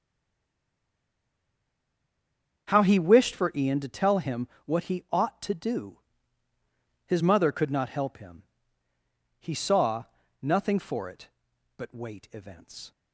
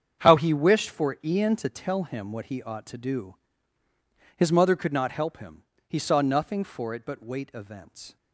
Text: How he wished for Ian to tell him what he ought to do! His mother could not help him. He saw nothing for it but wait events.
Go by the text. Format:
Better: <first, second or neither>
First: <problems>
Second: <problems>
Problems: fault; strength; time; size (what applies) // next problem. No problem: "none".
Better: second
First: stays silent before the first word; strong; until 2.6 s; 2.6 s long // starts louder than the rest; until 3.7 s; 6.5 dB // pauses between "him" and "what"; slight; at 4.4 s; 0.18 s long // pauses between "saw" and "nothing"; slight; at 10.0 s; 0.36 s long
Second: starts louder than the rest; strong; until 1.2 s; 7.5 dB